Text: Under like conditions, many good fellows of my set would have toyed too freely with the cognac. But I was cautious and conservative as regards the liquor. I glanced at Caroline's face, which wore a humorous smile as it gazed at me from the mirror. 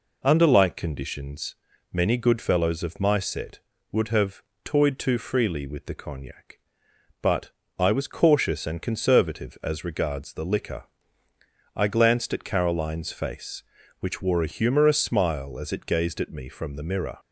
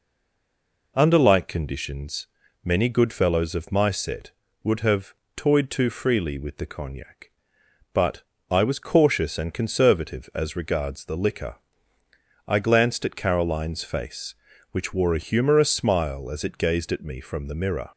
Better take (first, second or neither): first